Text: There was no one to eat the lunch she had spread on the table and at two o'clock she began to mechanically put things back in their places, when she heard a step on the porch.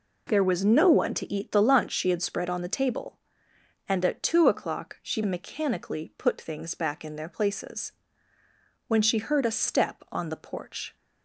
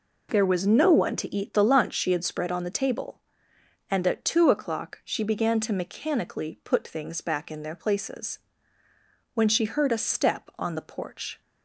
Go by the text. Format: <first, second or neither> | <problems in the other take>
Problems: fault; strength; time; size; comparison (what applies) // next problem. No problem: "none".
second | skips "began to"; at 5.2 s